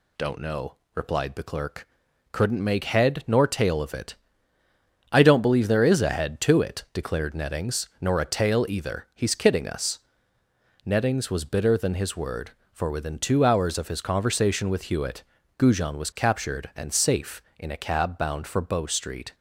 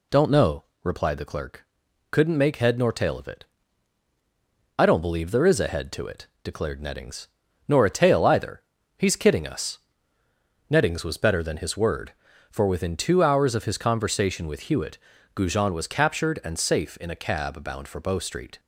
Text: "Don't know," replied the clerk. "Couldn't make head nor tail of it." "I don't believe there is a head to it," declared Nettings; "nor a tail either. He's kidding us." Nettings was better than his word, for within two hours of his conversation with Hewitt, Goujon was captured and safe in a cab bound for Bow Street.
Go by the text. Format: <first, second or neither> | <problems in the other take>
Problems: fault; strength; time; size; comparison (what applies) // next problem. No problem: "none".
second | says "bitter" for "better"; at 11.4 s